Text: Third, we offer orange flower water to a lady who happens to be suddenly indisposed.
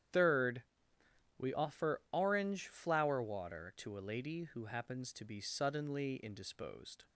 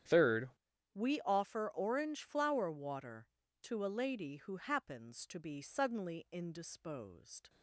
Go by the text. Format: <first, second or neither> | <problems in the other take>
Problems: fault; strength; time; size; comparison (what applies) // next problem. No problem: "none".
first | starts louder than the rest; strong; until 1.5 s; 9.5 dB; strong in the first // changes voice at "we"; from 0.9 s on; 6.5 s long